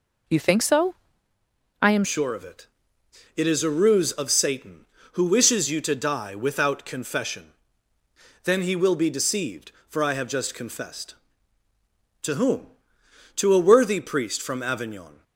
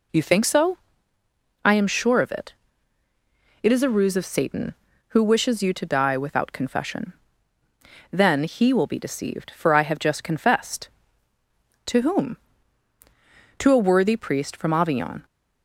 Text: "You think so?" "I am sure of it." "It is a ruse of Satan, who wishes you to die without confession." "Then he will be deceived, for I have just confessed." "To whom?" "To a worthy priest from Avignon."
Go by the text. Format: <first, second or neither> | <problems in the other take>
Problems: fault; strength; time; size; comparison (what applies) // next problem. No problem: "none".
second | changes voice at "sure"; from 2.0 s on; 13.2 s long